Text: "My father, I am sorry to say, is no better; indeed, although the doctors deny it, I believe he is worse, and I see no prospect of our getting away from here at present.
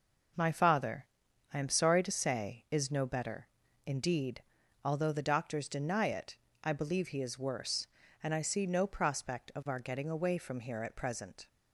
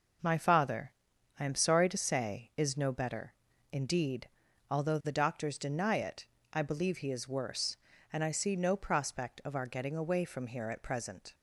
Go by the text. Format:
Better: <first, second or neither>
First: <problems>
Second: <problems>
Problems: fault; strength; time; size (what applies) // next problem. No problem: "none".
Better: neither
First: none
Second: none